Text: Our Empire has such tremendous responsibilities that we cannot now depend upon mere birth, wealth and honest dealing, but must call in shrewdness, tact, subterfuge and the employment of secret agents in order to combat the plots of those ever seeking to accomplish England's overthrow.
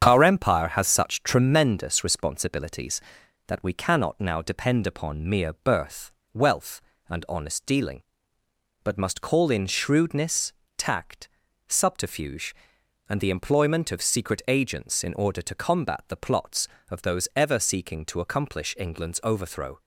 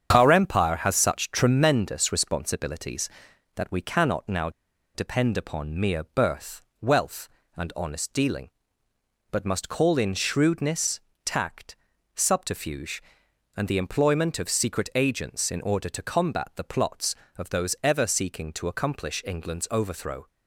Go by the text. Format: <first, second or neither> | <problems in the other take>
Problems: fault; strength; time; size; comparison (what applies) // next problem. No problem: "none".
first | starts louder than the rest; strong; until 1.1 s; 7.5 dB; strong in the first // pauses between "now" and "depend"; at 4.4 s; 0.45 s long